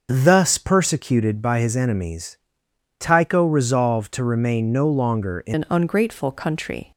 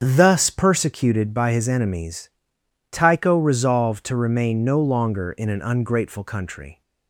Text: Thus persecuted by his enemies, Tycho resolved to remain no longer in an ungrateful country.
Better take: second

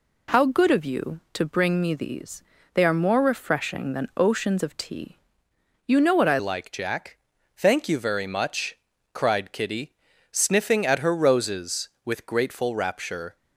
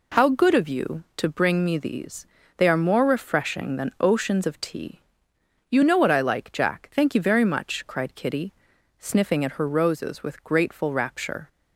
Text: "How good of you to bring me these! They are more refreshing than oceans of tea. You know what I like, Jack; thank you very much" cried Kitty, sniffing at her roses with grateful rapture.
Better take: second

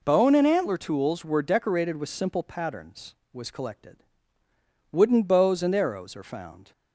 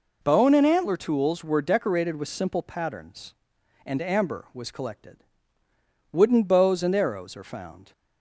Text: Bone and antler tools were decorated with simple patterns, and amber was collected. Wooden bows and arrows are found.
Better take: second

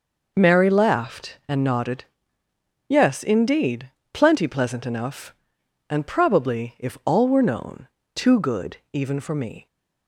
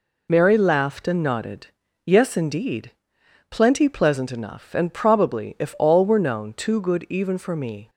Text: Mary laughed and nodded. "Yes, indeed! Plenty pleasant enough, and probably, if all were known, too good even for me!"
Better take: neither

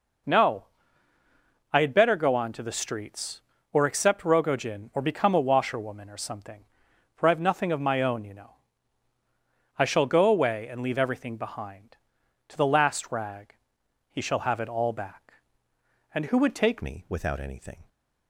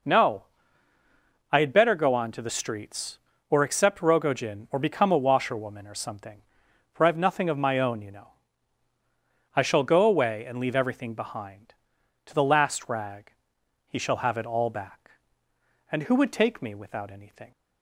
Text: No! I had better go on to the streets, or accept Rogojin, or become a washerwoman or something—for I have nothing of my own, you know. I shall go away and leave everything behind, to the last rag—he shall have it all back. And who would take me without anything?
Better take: second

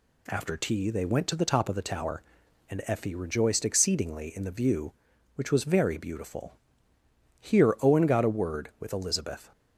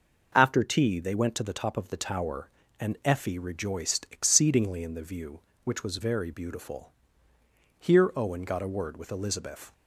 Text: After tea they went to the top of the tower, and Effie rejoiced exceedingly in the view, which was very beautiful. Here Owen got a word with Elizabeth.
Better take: neither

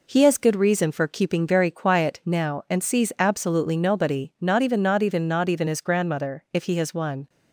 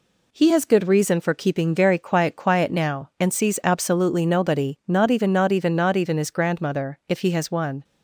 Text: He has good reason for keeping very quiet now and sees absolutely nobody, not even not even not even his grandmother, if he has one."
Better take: first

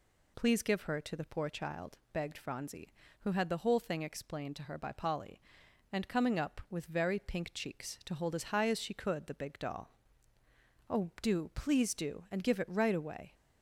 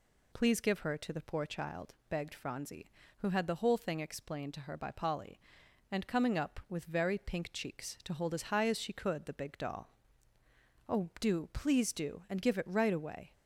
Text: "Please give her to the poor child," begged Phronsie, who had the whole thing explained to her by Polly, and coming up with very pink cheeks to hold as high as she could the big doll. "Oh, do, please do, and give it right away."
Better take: neither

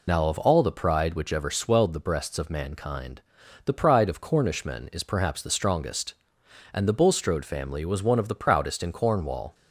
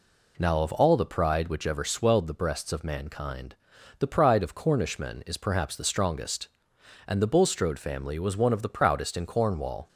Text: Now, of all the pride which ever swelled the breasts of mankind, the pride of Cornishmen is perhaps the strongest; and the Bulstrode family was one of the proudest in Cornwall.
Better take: second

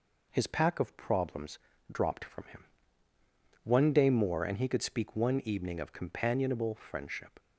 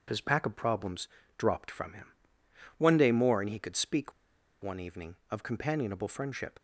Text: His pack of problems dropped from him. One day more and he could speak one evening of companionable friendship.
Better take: first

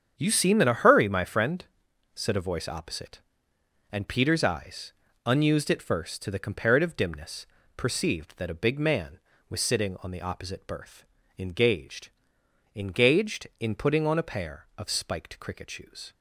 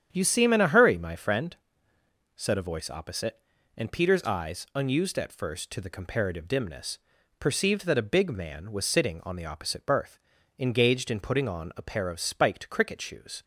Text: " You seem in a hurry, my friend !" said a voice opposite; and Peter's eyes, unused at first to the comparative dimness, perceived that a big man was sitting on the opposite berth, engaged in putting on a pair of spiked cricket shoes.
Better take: second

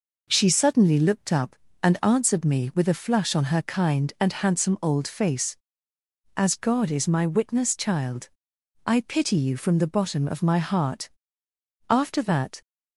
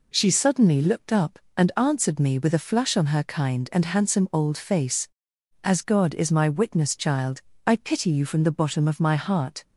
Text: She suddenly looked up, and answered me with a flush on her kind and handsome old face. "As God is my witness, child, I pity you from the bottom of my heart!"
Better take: second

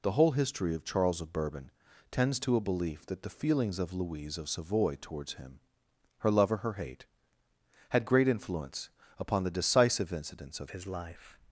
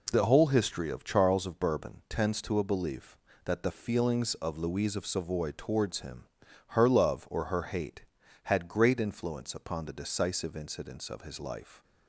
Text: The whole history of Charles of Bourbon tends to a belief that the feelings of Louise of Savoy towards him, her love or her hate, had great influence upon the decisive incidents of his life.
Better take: second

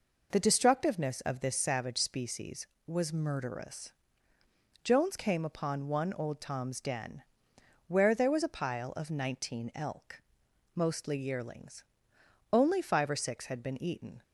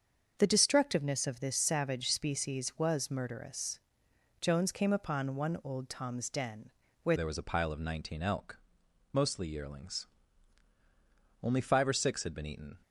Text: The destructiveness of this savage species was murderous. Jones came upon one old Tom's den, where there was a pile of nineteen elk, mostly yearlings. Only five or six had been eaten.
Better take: first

